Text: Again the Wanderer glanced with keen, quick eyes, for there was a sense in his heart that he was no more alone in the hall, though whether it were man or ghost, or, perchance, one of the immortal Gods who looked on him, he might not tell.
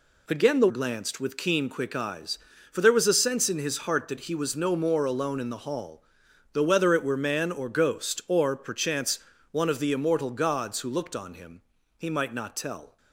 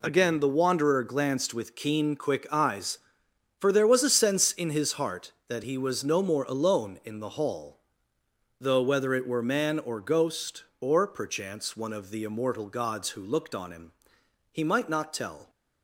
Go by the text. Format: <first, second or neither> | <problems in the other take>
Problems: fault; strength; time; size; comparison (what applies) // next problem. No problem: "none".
second | skips "Wanderer"; at 0.6 s